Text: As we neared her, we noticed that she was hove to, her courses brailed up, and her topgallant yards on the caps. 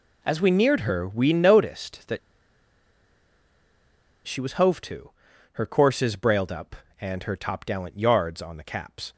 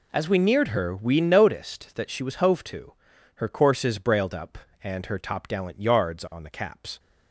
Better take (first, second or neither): second